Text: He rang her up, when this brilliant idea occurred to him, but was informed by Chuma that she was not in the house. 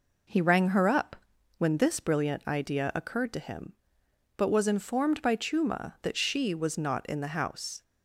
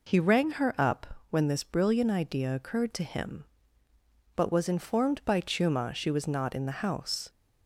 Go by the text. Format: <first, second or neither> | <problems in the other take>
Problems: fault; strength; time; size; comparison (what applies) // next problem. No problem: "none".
first | skips "that"; at 5.9 s